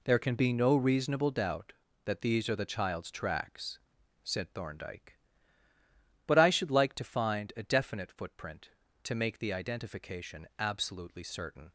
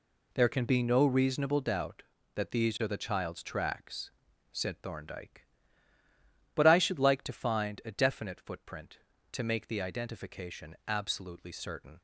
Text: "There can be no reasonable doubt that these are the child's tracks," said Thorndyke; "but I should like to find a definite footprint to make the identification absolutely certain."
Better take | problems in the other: neither | none

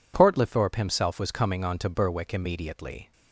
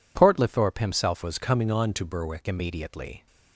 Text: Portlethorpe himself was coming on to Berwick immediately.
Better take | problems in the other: first | changes voice from "was" to "Berwick"; from 1.2 to 2.4 s; 1.2 s long

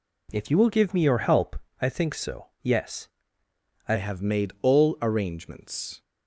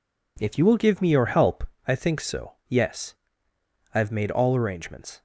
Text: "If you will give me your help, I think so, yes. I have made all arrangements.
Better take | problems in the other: second | changes voice at "have"; from 3.9 s on; 2.1 s long

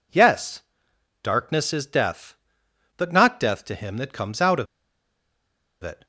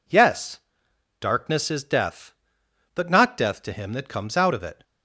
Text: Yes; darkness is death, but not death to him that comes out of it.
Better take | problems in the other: second | pauses between "of" and "it"; at 4.6 s; 1.1 s long

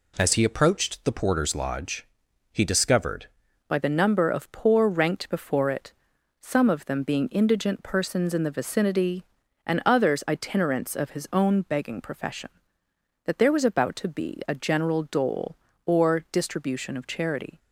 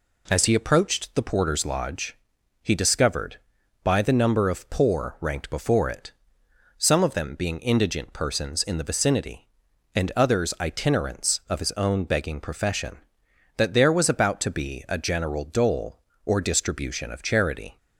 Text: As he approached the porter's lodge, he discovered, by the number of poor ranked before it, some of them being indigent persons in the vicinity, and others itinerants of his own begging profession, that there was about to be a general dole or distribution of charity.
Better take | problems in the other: second | changes voice at "by"; from 3.6 s on; 13.9 s long

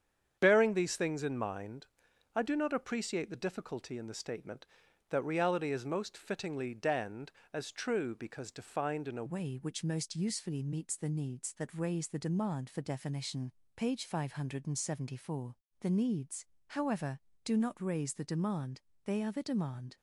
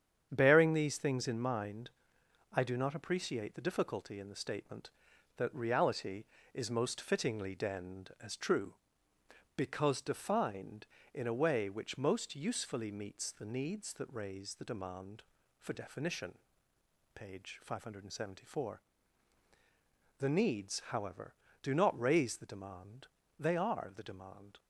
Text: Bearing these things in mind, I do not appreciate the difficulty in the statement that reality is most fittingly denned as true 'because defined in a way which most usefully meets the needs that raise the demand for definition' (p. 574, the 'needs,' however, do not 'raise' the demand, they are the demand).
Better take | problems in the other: second | starts louder than the rest; strong; until 1.4 s; 8 dB; strong in the second // changes voice at "way"; from 9.2 s on; 10.7 s long

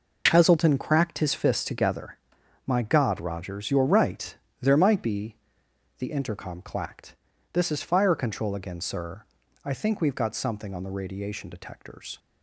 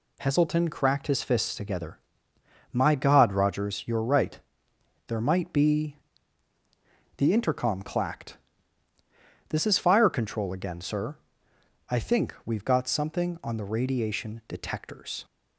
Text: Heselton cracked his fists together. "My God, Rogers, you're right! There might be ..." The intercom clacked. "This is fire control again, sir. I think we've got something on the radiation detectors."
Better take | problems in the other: neither | none

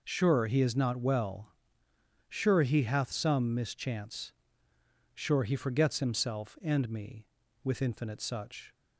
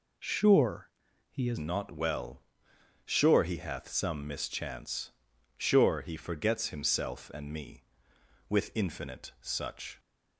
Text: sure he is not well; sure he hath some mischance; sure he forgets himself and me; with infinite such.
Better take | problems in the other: first | pauses between "sure" and "he"; at 0.9 s; 0.40 s long // changes voice at "not"; from 1.5 s on; 8.4 s long

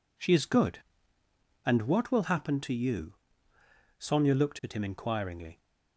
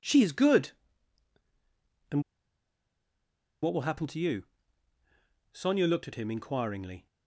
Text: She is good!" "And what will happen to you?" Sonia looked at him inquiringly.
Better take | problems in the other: first | pauses between "And" and "what"; strong; at 2.2 s; 1.4 s long

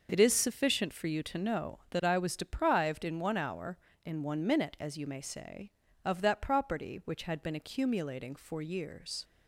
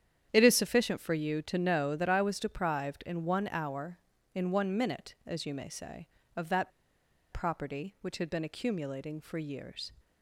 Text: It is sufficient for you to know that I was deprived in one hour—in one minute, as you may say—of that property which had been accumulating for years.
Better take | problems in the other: first | starts louder than the rest; strong; until 1.3 s; 9.5 dB // pauses between "that" and "property"; noticeable; at 6.7 s; 0.61 s long

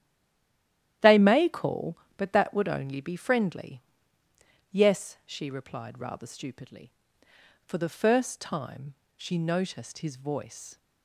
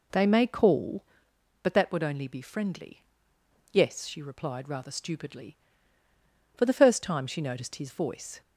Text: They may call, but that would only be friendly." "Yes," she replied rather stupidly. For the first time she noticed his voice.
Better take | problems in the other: second | stays silent before the first word; until 1.0 s; 1.0 s long // starts louder than the rest; strong; until 2.2 s; 12 dB // pauses between "time" and "she"; slight; at 8.9 s; 0.20 s long

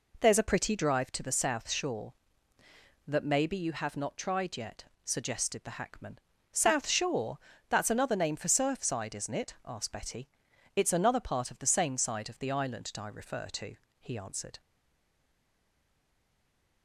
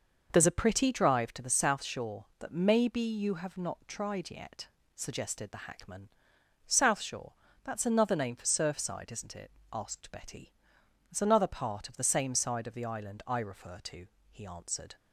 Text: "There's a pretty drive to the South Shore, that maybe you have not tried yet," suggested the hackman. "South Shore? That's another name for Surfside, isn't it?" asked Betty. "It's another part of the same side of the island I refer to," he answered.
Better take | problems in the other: second | stays silent after the last word; from 14.5 s on; 2.3 s long

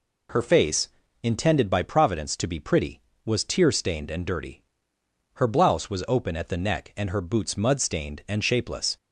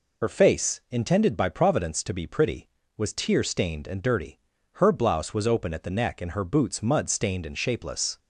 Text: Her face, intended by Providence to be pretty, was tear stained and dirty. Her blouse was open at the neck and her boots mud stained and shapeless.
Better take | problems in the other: first | loses the start of "Her"; at 0.2 s; 45 ms

